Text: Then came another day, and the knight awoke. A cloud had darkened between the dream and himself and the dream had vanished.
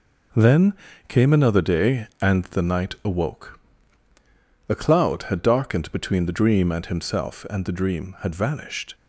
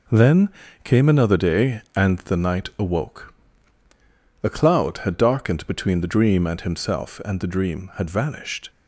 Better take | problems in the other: neither | pauses between "Then" and "came"; slight; the same in both

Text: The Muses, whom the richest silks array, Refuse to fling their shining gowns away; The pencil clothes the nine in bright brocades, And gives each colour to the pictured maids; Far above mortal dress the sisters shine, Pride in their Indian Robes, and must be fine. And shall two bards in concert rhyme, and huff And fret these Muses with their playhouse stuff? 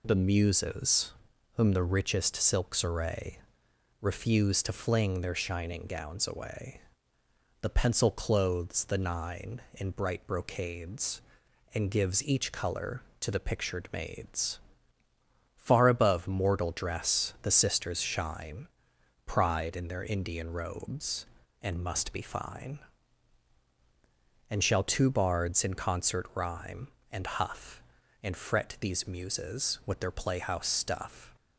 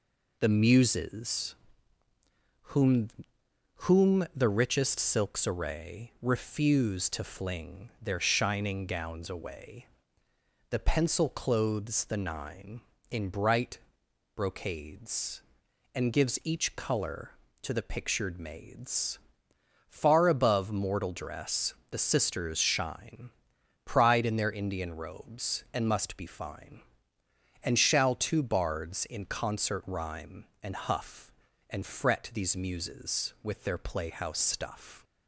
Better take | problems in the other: first | says "whom" twice; at 3.8 s // pauses between "bright" and "brocades"; noticeable; at 13.7 s; 0.56 s long // pauses between "dress" and "the"; slight; at 21.7 s; 0.16 s long

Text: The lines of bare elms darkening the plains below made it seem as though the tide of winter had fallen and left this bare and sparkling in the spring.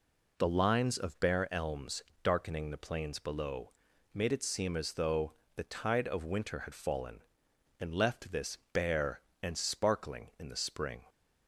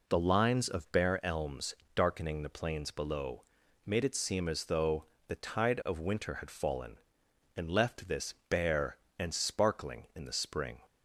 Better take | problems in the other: neither | pauses between "elms" and "darkening"; slight; the same in both // pauses between "below" and "made"; the same in both // pauses between "though" and "the"; slight; the same in both // pauses between "this" and "bare"; slight; the same in both

